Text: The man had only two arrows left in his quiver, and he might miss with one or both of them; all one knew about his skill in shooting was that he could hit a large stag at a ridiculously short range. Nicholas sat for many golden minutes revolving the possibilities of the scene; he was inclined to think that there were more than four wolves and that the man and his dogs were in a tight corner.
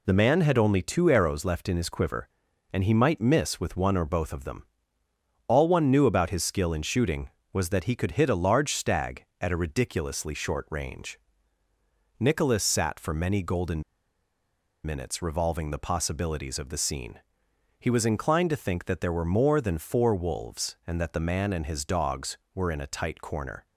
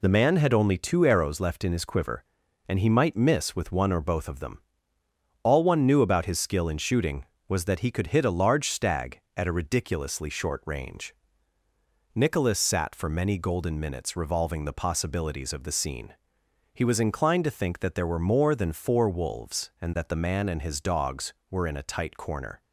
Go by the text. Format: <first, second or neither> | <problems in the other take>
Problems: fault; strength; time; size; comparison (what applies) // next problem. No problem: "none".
second | pauses between "golden" and "minutes"; at 13.8 s; 1.0 s long